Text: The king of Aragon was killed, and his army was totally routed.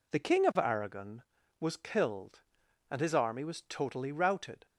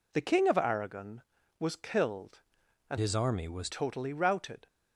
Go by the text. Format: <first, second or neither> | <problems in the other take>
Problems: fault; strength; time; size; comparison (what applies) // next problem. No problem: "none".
first | changes voice from "his" to "was"; from 2.9 to 3.7 s; 0.8 s long